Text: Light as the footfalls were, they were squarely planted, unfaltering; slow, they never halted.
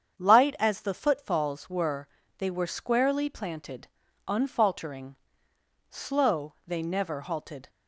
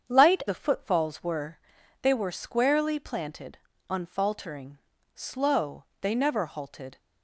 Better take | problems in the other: first | starts louder than the rest; strong; until 1.1 s; 7.5 dB; strong in the first // skips "as"; at 0.4 s

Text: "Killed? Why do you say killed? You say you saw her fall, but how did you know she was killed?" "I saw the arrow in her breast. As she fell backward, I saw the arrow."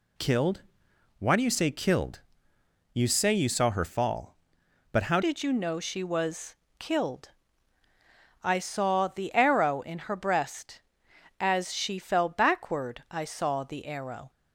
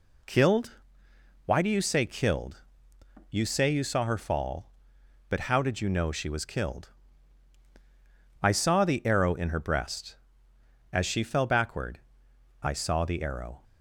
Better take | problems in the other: second | changes voice at "did"; from 5.2 s on; 9.1 s long // pauses between "was" and "killed"; slight; at 6.5 s; 0.22 s long

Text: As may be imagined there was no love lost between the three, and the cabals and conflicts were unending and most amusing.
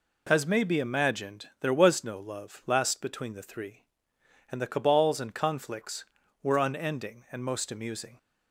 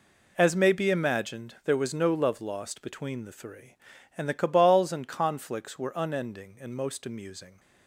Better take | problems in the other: second | pauses between "imagined" and "there"; slight; at 1.4 s; 0.16 s long // says "last" for "lost"; at 2.6 s

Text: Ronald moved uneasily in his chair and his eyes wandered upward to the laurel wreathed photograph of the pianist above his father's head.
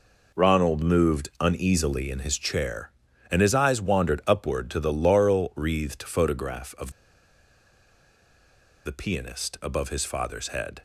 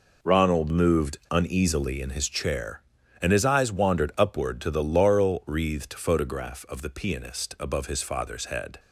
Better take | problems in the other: second | pauses between "of" and "the"; strong; at 6.9 s; 1.9 s long

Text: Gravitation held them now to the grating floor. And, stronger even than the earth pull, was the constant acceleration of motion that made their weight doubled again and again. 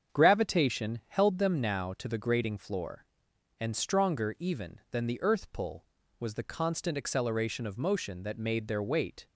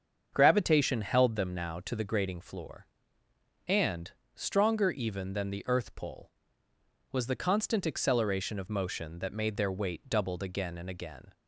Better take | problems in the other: second | starts louder than the rest; strong; until 1.2 s; 7.5 dB; also in the second // stops before "doubled again and again"; at 9.2 s

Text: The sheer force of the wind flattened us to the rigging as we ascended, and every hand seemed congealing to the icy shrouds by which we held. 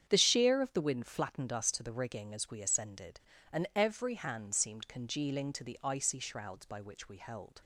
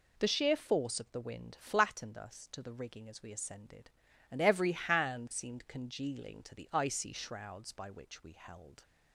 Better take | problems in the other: second | starts louder than the rest; strong; until 1.1 s; 8.5 dB // skips "force"; at 0.6 s

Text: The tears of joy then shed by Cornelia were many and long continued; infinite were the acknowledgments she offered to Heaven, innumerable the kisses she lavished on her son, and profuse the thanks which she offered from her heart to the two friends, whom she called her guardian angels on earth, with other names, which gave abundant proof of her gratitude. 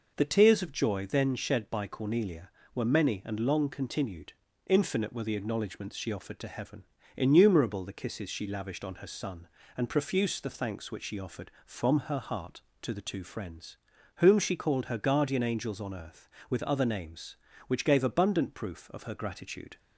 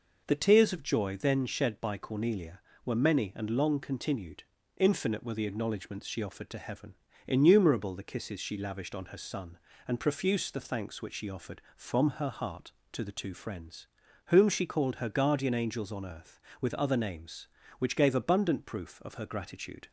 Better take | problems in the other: neither | none

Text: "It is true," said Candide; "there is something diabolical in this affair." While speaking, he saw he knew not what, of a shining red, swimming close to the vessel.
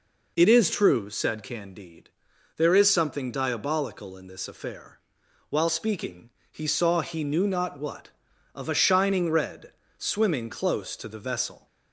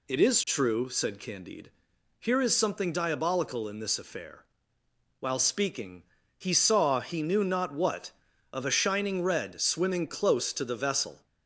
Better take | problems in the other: first | says "here" for "there"; at 2.1 s

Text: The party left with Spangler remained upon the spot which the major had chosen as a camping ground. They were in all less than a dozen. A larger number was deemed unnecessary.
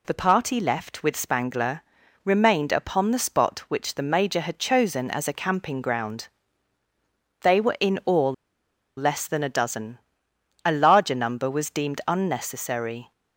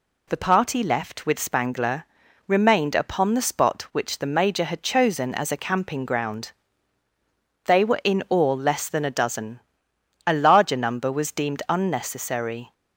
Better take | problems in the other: second | pauses between "Spangler" and "remained"; at 1.8 s; 0.44 s long; also in the second // pauses between "all" and "less"; noticeable; at 8.3 s; 0.64 s long

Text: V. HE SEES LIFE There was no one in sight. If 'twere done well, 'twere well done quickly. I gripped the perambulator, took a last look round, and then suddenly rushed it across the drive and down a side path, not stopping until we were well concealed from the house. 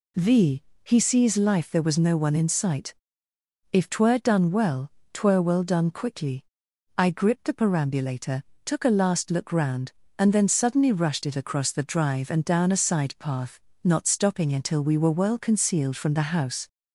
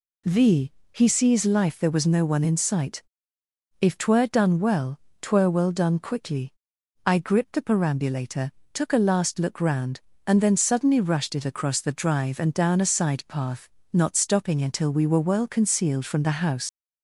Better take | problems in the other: first | leaves "house" unfinished; at 16.6 s; 75 ms

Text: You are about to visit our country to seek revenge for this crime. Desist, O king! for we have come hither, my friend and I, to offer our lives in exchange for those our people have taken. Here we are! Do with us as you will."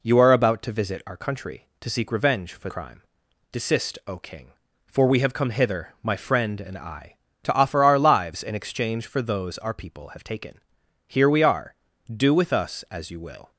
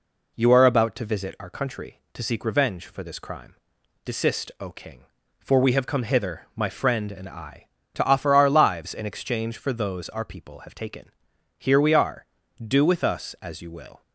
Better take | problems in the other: second | skips "this"; at 2.6 s

